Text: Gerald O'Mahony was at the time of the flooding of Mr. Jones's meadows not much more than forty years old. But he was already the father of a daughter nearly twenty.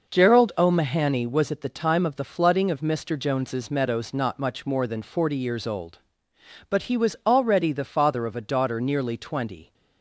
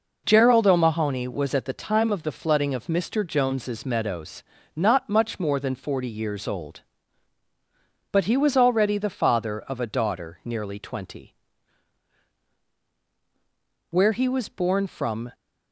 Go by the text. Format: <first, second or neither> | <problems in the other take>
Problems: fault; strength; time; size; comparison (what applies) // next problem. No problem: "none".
first | pauses between "meadows" and "not"; slight; at 4.4 s; 0.32 s long // goes on to say "Where he was born from"; from 13.8 s on; 1.4 s long